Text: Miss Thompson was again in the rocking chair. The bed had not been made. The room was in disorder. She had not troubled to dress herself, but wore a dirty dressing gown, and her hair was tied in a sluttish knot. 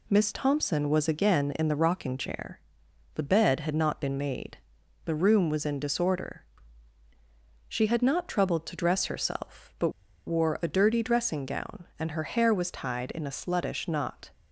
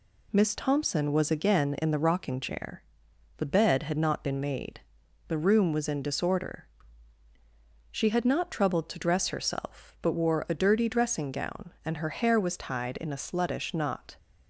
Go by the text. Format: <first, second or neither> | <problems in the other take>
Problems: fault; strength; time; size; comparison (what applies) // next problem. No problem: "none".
second | pauses between "but" and "wore"; at 9.8 s; 0.37 s long